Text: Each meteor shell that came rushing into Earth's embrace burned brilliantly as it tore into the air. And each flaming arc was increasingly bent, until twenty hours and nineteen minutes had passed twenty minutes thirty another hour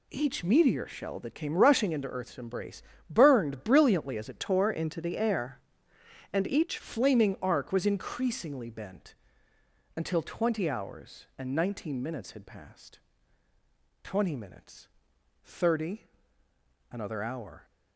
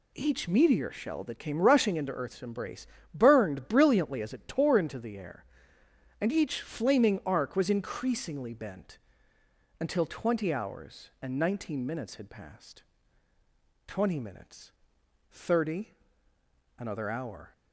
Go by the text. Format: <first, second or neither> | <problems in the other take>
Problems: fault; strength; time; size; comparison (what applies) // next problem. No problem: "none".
second | pauses between "embrace" and "burned"; slight; at 2.8 s; 0.26 s long; slight in the second // changes voice from "tore" to "each"; from 4.3 to 6.7 s; 2.4 s long // pauses between "passed" and "twenty"; at 12.9 s; 1.0 s long; also in the second // pauses between "minutes" and "thirty"; noticeable; at 14.8 s; 0.56 s long; noticeable in the second // pauses between "thirty" and "another"; noticeable; at 16.0 s; 0.90 s long; noticeable in the second